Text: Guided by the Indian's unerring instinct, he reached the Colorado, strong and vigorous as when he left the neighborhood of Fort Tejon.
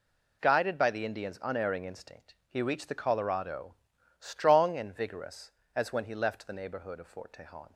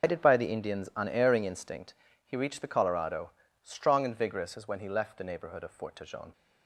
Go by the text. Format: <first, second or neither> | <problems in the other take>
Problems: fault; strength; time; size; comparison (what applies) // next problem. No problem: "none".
first | loses the start of "Guided"; at 0.0 s; 155 ms